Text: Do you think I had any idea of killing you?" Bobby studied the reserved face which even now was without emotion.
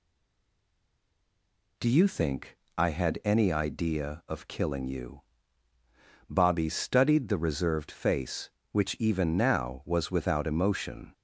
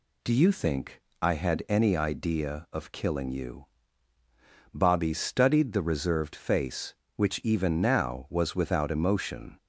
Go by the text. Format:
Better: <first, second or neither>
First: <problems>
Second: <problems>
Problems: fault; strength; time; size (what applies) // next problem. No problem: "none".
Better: second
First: stays silent before the first word; noticeable; until 1.7 s; 1.7 s long // pauses between "think" and "I"; slight; at 2.5 s; 0.18 s long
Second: pauses between "think" and "I"; slight; at 1.0 s; 0.18 s long